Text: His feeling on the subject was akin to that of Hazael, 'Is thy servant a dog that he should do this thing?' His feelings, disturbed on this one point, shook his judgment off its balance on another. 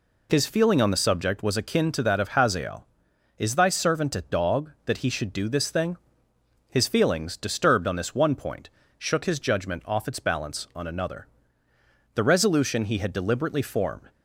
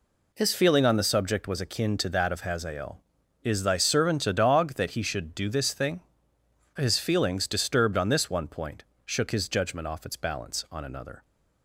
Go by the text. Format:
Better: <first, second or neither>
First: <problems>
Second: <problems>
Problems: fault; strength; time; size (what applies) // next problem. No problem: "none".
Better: second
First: goes on to say "The resolution he had deliberately formed"; strong; from 12.1 s on; 1.9 s long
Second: none